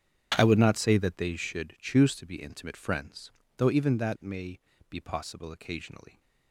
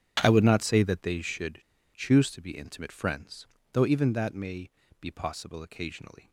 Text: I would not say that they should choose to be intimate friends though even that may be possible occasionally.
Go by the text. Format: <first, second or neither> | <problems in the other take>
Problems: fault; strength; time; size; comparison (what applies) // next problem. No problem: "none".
first | starts louder than the rest; strong; until 1.2 s; 9.5 dB; strong in the first // pauses between "should" and "choose"; slight; at 1.6 s; 0.34 s long // pauses between "friends" and "though"; slight; at 3.4 s; 0.28 s long; slight in the first // pauses between "may" and "be"; slight; at 4.7 s; 0.30 s long; slight in the first